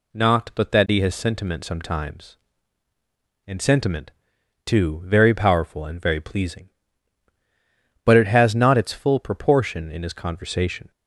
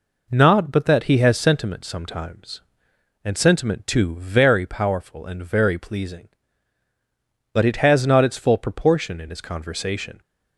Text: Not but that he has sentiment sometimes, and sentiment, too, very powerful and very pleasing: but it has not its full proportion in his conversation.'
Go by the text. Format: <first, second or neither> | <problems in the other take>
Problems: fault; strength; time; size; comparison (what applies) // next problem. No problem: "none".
first | gets quieter; noticeable; throughout; 4 dB